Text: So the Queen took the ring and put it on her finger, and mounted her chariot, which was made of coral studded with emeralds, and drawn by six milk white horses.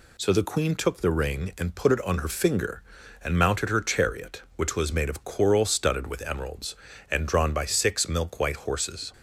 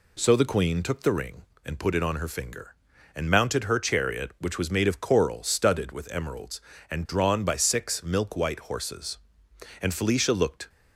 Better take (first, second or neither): first